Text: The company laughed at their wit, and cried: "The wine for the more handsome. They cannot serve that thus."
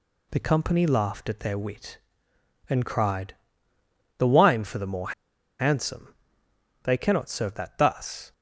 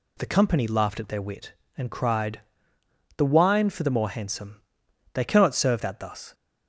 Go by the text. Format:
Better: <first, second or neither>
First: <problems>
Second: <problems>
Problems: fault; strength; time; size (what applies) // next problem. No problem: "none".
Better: second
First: pauses between "more" and "handsome"; noticeable; at 5.1 s; 0.48 s long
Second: none